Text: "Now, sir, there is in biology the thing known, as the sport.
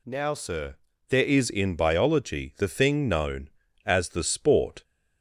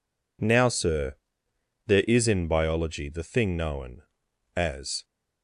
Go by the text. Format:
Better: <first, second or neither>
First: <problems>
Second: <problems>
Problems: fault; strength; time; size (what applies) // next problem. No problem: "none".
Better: first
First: none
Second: stops before "the sport"; at 5.0 s